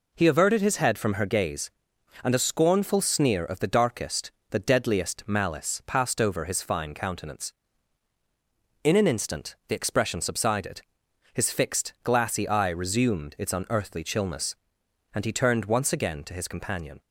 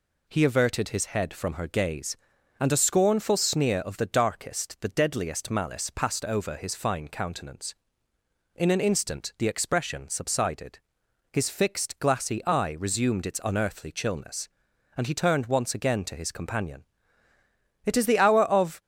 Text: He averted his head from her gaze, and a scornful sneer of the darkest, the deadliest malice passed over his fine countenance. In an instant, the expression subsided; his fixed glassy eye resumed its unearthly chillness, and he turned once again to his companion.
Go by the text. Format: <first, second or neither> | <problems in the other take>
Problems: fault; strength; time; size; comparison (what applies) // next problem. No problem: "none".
first | goes on to say "It is the hour of"; noticeable; from 17.8 s on; 0.96 s long